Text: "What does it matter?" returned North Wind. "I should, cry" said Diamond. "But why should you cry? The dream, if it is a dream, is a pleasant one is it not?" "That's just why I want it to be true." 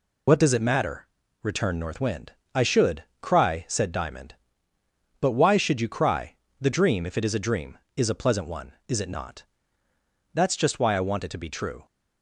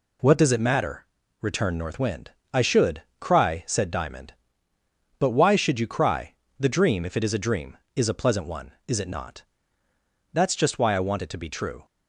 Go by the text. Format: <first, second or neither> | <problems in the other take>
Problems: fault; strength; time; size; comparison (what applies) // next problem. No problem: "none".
second | loses the start of "What"; at 0.2 s; 60 ms